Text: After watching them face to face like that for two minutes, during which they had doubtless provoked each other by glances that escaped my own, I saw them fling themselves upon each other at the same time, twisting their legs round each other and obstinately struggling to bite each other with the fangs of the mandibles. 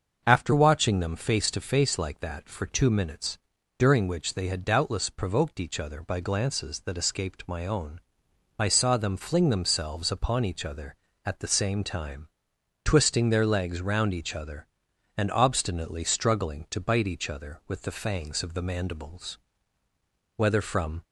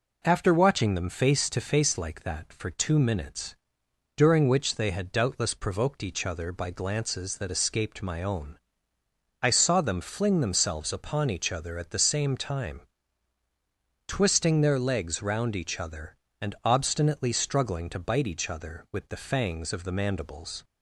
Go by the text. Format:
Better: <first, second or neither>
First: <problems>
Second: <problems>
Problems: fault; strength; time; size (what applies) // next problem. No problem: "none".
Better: second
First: starts louder than the rest; until 1.2 s; 6.5 dB // goes on to say "Whether from"; noticeable; from 20.3 s on; 0.66 s long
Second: none